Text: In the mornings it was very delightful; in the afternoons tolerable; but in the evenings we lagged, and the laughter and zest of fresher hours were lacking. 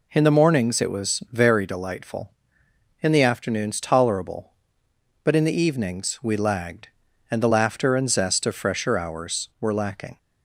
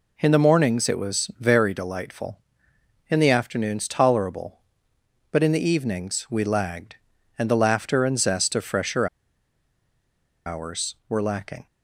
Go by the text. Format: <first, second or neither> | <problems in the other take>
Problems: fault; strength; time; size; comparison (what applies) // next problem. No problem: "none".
first | pauses between "fresher" and "hours"; strong; at 9.0 s; 1.3 s long